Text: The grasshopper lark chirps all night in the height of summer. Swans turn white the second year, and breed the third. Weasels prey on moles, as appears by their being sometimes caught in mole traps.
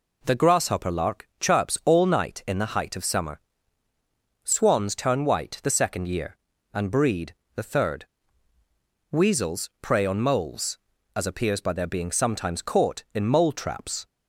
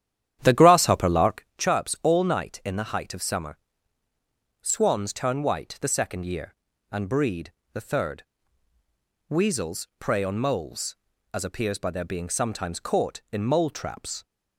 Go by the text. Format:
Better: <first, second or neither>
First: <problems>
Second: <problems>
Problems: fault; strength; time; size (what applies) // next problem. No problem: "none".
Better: first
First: pauses between "breed" and "the"; slight; at 7.3 s; 0.22 s long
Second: starts louder than the rest; strong; until 1.6 s; 10.5 dB // pauses between "breed" and "the"; slight; at 7.5 s; 0.22 s long